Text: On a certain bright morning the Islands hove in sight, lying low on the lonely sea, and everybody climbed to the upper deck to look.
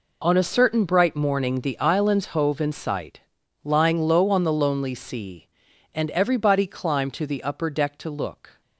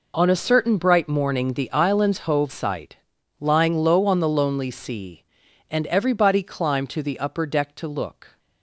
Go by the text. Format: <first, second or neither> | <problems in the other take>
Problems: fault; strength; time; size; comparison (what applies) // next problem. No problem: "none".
first | skips "in"; at 2.4 s